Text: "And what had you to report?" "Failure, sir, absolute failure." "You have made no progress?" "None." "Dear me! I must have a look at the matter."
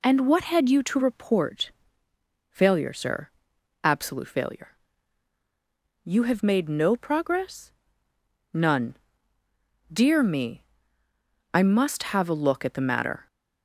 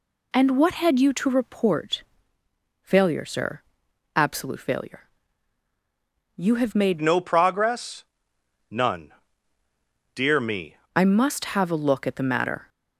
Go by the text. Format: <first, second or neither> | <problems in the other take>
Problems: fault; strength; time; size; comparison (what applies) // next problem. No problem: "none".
first | changes voice from "no" to "me"; from 7.0 to 10.7 s; 3.7 s long